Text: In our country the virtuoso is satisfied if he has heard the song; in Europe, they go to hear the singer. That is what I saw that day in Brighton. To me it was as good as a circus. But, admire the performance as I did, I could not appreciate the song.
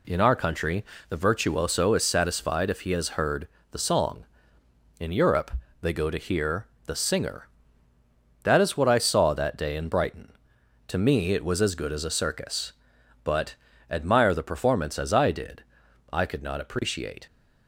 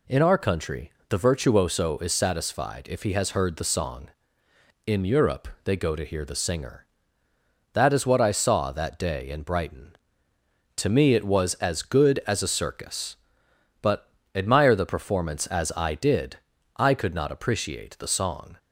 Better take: second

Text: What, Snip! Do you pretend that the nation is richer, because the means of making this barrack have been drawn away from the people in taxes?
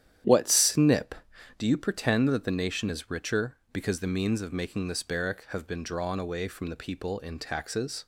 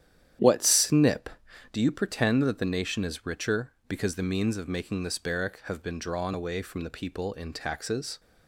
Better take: neither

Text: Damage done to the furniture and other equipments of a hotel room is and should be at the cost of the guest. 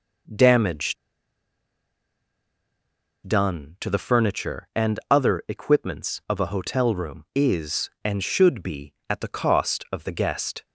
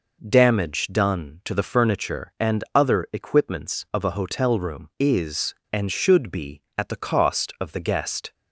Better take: second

